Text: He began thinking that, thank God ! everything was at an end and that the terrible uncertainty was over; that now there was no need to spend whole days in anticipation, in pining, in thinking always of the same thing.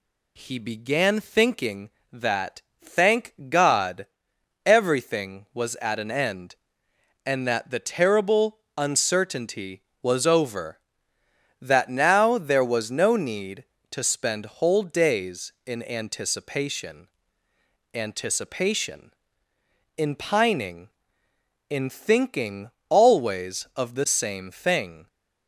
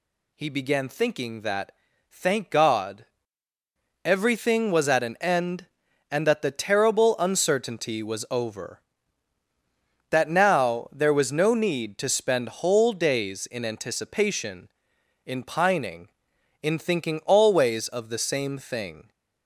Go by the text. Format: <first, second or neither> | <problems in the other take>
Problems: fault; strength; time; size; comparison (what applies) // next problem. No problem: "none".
second | pauses between "thank" and "God"; slight; at 3.3 s; 0.16 s long // pauses between "terrible" and "uncertainty"; slight; at 8.5 s; 0.18 s long // says "anticipation" twice; at 17.9 s // pauses between "thinking" and "always"; slight; at 22.6 s; 0.22 s long